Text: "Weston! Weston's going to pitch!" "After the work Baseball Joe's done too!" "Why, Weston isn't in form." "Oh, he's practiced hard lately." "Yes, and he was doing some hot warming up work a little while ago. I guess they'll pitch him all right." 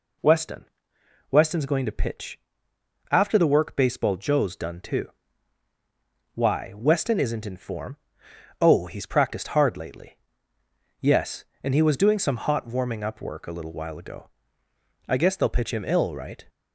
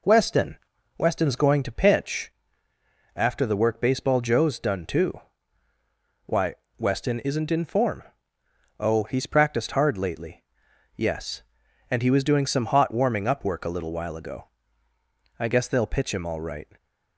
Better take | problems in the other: second | says "ill" for "all"; at 15.8 s

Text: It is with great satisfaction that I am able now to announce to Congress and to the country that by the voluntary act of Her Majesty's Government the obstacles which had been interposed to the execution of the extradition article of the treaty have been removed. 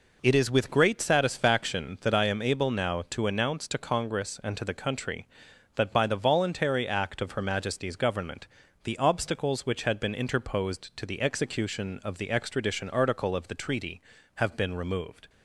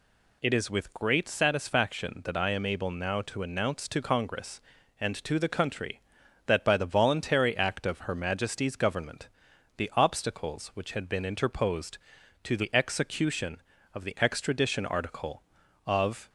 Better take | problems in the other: first | pauses between "Government" and "the"; noticeable; at 9.2 s; 0.48 s long; also in the first // stops before "the treaty have been removed"; at 16.2 s

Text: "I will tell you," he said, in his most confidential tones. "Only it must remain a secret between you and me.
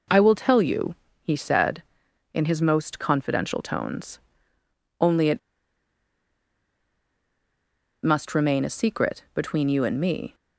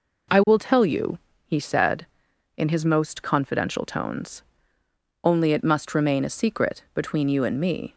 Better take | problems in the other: second | pauses between "it" and "must"; strong; at 5.3 s; 2.6 s long

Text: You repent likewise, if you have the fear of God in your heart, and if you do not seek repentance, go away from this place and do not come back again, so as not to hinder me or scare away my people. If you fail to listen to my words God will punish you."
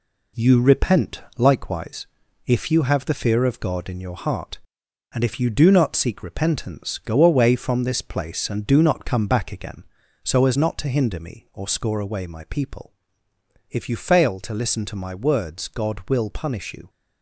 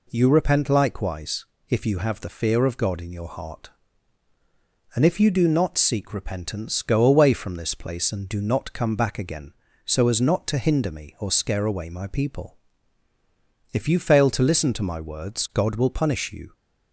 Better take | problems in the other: second | pauses between "repent" and "likewise"; slight; at 1.2 s; 0.16 s long // says "score" for "scare"; at 11.6 s

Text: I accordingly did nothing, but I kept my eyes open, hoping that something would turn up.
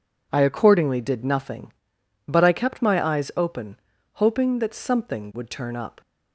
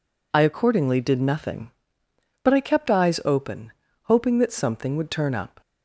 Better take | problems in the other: first | skips "my"; at 2.9 s

